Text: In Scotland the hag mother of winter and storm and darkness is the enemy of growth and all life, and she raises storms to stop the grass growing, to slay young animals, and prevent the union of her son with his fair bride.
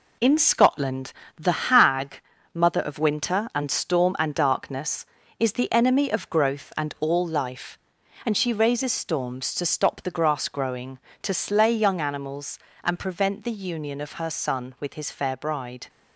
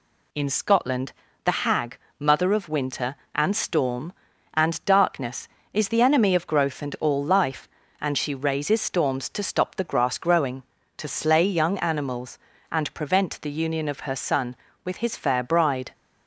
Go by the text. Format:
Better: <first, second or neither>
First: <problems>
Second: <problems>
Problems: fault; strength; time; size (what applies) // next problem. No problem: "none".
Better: second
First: gets quieter; throughout; 6.5 dB // pauses between "Scotland" and "the"; slight; at 1.1 s; 0.22 s long // pauses between "hag" and "mother"; slight; at 2.2 s; 0.34 s long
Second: pauses between "Scotland" and "the"; slight; at 1.1 s; 0.32 s long // pauses between "hag" and "mother"; slight; at 1.9 s; 0.24 s long